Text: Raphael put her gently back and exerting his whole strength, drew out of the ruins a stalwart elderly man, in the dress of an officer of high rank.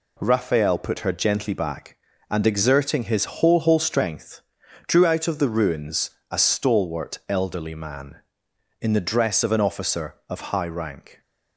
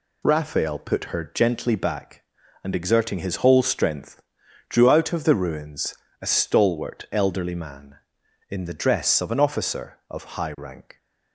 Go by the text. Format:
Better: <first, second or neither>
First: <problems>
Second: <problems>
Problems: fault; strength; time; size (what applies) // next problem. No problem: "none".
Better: second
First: says "whole" twice; at 3.5 s // pauses between "ruins" and "a"; slight; at 6.0 s; 0.22 s long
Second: pauses between "ruins" and "a"; slight; at 5.9 s; 0.26 s long